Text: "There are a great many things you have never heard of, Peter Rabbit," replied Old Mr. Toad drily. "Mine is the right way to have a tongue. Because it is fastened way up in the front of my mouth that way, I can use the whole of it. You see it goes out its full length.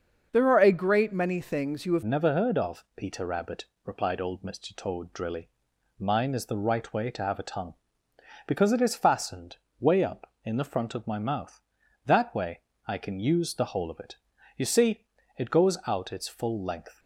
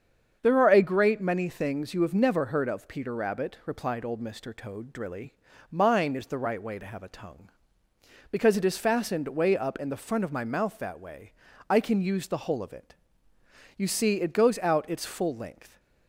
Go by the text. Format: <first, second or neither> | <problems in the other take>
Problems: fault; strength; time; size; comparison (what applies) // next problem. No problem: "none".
second | starts louder than the rest; until 1.3 s; 6.5 dB; strong in the second // changes voice at "never"; from 2.0 s on; 14.9 s long // pauses between "fastened" and "way"; slight; at 9.5 s; 0.24 s long // pauses between "see" and "it"; slight; at 15.0 s; 0.32 s long